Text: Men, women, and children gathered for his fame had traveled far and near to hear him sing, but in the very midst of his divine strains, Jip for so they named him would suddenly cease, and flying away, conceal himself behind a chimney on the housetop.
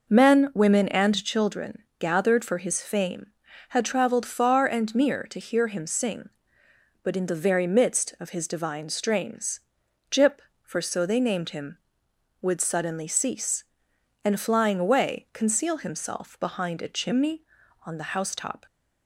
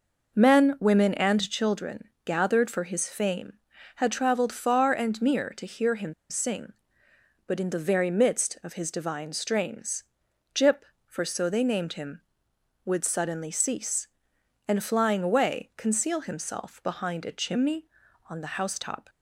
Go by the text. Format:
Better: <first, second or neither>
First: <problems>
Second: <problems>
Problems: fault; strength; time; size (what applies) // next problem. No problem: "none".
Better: first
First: pauses between "children" and "gathered"; slight; at 1.8 s; 0.18 s long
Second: pauses between "children" and "gathered"; slight; at 2.0 s; 0.18 s long // pauses between "him" and "sing"; slight; at 6.1 s; 0.16 s long